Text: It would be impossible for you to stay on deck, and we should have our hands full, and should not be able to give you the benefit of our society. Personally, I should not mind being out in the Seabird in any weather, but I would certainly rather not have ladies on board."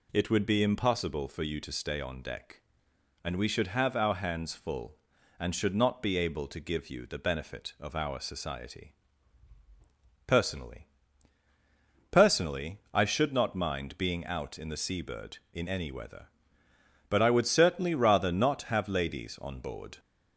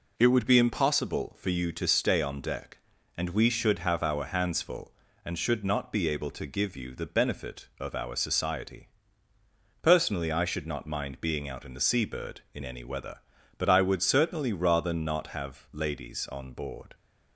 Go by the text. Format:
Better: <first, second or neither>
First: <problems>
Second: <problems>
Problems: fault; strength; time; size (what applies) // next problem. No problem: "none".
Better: second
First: says "Personally" twice; at 12.1 s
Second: none